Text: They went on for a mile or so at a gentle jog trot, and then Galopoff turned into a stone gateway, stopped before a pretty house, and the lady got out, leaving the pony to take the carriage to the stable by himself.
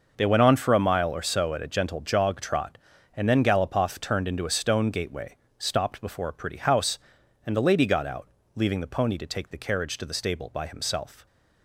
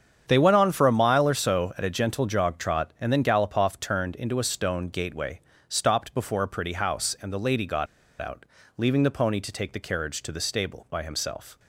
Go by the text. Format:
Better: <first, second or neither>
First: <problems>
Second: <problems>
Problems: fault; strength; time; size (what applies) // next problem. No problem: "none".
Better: first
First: none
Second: starts louder than the rest; strong; until 1.2 s; 8 dB // pauses between "got" and "out"; slight; at 7.8 s; 0.32 s long